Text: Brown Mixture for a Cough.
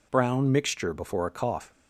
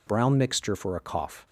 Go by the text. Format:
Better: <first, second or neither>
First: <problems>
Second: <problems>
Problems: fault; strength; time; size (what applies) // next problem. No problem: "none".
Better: second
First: says "before" for "for"; at 0.9 s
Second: none